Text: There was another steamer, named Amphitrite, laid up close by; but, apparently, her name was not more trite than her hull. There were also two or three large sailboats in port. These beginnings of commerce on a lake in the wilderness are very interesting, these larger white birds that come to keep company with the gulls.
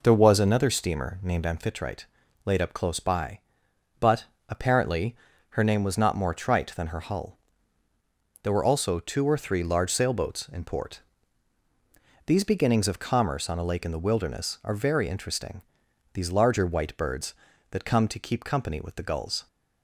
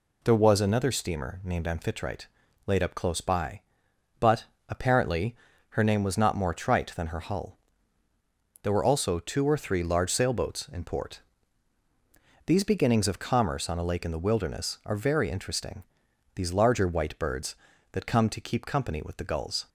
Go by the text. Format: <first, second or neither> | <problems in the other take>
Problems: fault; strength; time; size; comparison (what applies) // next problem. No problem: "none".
second | starts louder than the rest; noticeable; until 1.6 s; 4.5 dB